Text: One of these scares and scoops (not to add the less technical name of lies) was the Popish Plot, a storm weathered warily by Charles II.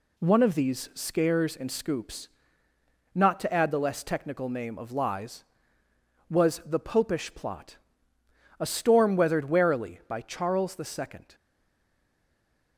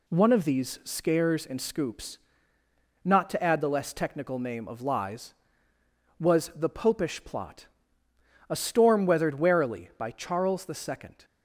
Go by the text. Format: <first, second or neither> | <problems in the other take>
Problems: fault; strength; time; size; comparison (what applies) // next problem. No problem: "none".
second | stays silent after the last word; noticeable; from 11.3 s on; 1.4 s long